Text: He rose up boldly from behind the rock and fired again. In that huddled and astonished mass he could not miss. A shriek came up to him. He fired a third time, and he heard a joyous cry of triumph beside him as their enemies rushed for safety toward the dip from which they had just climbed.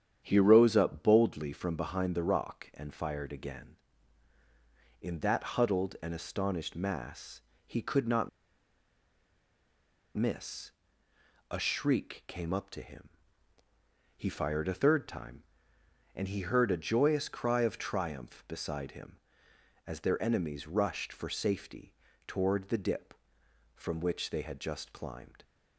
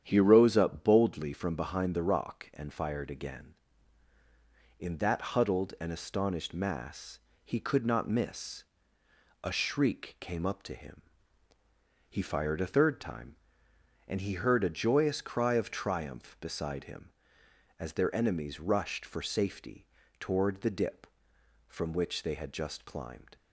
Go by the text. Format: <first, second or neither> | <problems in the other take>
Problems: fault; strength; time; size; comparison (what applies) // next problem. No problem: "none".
second | starts louder than the rest; strong; until 1.2 s; 9 dB; strong in the second // pauses between "mass" and "he"; slight; at 7.4 s; 0.26 s long; slight in the second // pauses between "not" and "miss"; strong; at 8.2 s; 1.8 s long // pauses between "safety" and "toward"; slight; at 21.9 s; 0.34 s long; slight in the second